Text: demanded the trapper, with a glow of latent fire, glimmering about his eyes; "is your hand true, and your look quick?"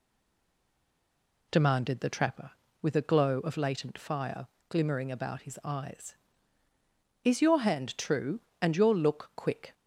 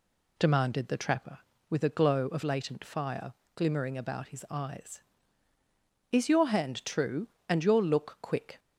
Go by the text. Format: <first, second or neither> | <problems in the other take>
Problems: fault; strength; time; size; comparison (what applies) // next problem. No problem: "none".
second | stays silent before the first word; noticeable; until 1.5 s; 1.5 s long